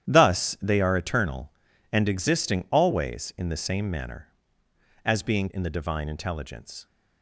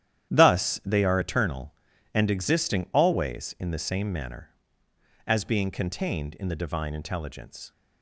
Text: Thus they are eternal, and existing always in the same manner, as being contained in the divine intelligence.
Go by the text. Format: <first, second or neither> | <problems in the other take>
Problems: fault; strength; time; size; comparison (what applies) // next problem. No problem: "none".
second | starts louder than the rest; strong; until 1.1 s; 10.5 dB; strong in the second // skips "contained"; at 5.4 s